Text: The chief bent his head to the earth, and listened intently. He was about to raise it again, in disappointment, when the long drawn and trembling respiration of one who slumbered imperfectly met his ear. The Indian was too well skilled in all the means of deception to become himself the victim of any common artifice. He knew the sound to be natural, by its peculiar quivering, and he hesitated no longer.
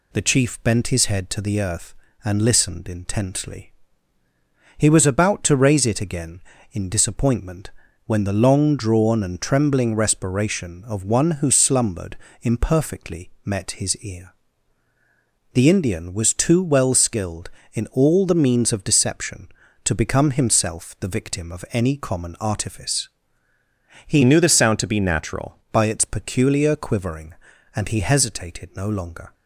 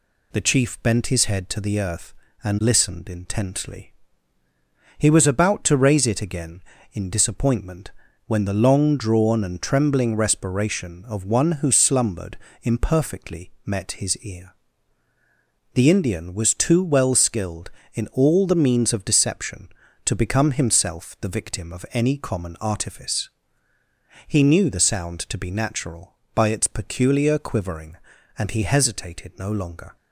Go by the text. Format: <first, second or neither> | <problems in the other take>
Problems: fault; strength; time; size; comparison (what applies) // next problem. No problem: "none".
second | pauses between "slumbered" and "imperfectly"; slight; at 12.1 s; 0.24 s long; slight in the second // pauses between "imperfectly" and "met"; slight; at 13.2 s; 0.16 s long; slight in the second // changes voice from "knew" to "natural"; from 24.2 to 25.5 s; 1.3 s long